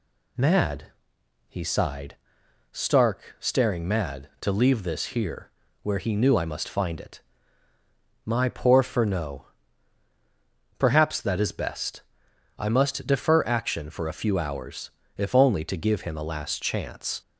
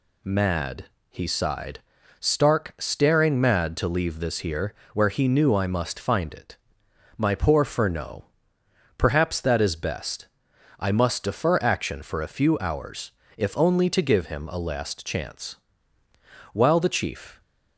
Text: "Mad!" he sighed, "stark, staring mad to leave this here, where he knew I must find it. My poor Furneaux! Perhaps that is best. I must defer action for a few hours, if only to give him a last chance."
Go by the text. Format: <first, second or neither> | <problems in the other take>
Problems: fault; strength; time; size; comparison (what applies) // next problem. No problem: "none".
first | goes on to say "While the Chief"; noticeable; from 16.5 s on; 0.88 s long